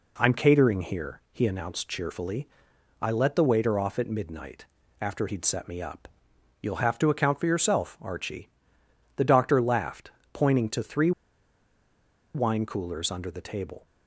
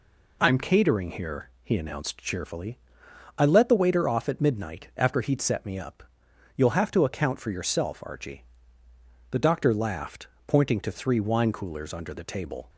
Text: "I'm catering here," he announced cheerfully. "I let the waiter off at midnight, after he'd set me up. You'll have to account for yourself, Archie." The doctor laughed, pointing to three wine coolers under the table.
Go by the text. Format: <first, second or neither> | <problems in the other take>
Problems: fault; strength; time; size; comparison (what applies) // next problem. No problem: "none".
second | pauses between "three" and "wine"; at 11.1 s; 1.2 s long